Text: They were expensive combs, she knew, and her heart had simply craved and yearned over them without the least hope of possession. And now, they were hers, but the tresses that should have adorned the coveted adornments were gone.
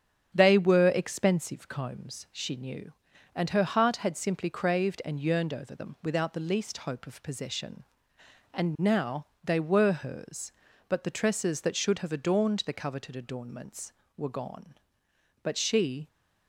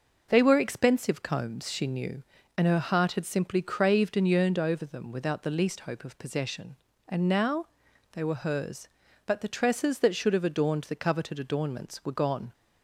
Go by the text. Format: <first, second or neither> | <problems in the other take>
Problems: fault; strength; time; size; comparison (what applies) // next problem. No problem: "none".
second | starts louder than the rest; strong; until 1.3 s; 8 dB // goes on to say "But she"; noticeable; from 15.4 s on; 0.66 s long